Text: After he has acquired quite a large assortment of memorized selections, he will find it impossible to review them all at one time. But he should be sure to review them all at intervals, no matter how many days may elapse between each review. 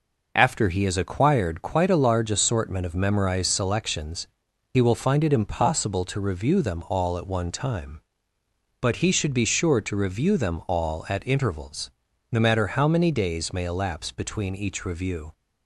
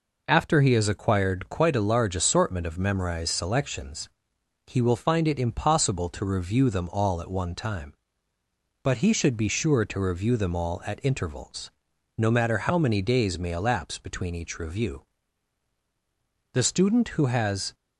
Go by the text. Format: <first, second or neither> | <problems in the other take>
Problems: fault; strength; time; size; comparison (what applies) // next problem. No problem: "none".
first | goes on to say "The student who has"; noticeable; from 16.5 s on; 1.2 s long